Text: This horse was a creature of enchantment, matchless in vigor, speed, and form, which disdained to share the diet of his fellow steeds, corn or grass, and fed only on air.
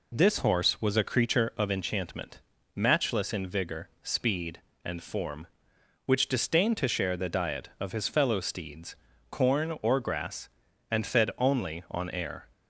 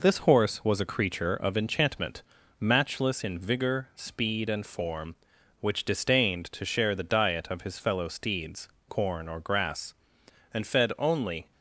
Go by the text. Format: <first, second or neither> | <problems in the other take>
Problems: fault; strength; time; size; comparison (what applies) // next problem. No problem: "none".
first | stops before "on air"; at 11.5 s